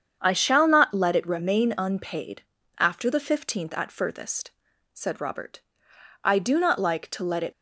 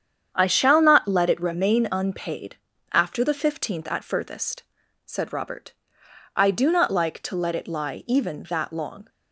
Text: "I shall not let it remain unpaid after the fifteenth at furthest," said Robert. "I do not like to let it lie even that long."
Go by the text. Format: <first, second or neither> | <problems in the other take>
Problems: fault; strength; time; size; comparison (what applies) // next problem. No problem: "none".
second | starts louder than the rest; strong; until 1.2 s; 7.5 dB; strong in the second // pauses between "unpaid" and "after"; slight; at 2.4 s; 0.36 s long; slight in the second // stops before "lie even that long"; at 7.5 s